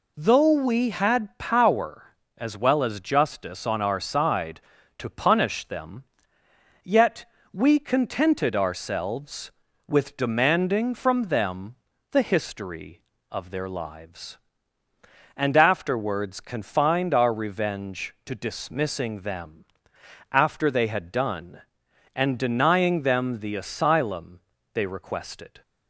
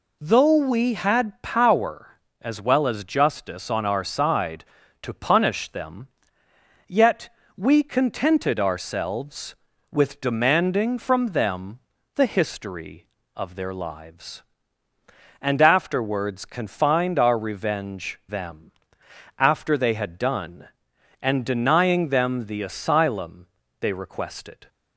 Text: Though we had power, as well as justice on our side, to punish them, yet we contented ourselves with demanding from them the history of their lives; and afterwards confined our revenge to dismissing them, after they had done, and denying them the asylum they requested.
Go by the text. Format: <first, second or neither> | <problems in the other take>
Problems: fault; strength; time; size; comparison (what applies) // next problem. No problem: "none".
first | pauses between "yet" and "we"; slight; at 7.2 s; 0.26 s long; slight in the first // pauses between "them" and "the"; slight; at 11.8 s; 0.34 s long; slight in the first // skips "to dismissing"; at 18.2 s // pauses between "asylum" and "they"; slight; at 23.4 s; 0.32 s long; slight in the first